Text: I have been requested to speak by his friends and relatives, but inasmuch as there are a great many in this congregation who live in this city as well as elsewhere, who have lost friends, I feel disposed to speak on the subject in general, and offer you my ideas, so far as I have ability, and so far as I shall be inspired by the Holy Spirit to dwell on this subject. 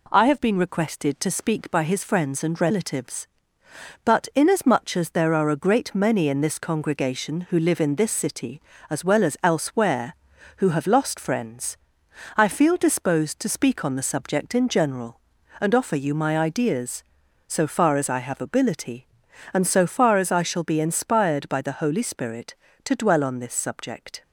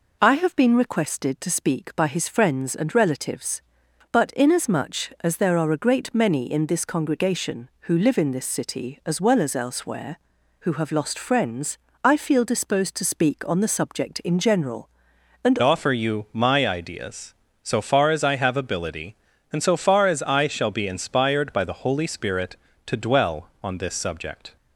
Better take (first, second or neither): first